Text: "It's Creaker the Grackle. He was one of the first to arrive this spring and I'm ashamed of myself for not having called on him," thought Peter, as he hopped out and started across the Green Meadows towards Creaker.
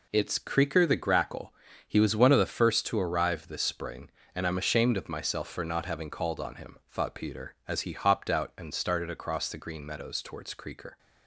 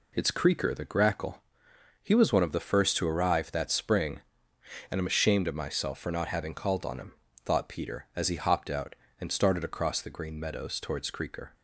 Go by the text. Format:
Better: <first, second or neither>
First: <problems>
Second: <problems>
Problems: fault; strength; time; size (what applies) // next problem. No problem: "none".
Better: first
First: none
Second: says "that" for "this"; at 3.5 s